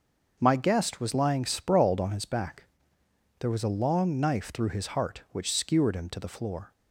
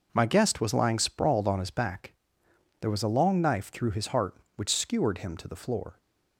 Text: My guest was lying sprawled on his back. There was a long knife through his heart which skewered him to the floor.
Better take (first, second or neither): neither